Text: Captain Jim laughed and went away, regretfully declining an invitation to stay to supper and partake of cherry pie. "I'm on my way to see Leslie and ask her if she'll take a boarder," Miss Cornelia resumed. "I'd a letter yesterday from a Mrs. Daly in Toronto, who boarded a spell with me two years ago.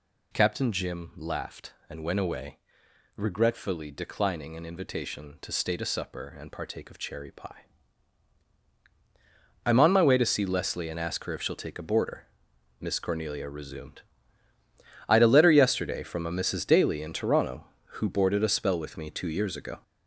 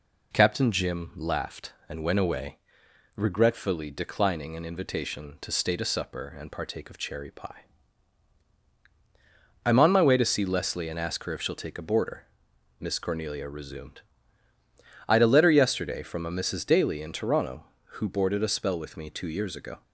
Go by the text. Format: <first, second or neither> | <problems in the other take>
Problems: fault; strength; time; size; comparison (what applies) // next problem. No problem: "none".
second | gets louder; noticeable; throughout; 6 dB